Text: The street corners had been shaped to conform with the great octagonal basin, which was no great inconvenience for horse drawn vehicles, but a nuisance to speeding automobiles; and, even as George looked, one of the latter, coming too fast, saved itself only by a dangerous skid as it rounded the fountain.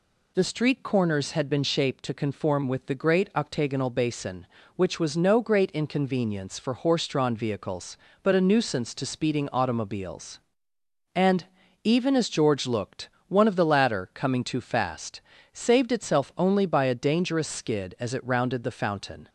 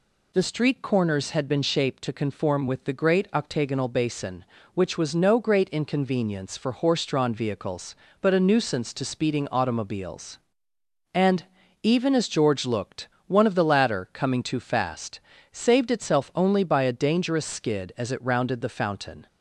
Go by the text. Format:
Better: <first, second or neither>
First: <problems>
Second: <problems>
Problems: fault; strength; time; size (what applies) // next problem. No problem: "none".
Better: neither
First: none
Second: none